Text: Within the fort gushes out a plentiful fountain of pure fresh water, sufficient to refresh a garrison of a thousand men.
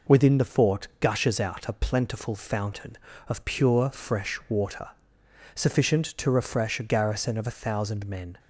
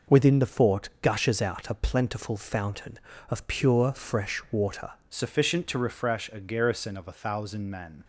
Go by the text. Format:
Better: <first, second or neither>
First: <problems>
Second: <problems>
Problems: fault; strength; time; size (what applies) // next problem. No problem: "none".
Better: first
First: none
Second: changes voice at "sufficient"; from 5.1 s on; 2.9 s long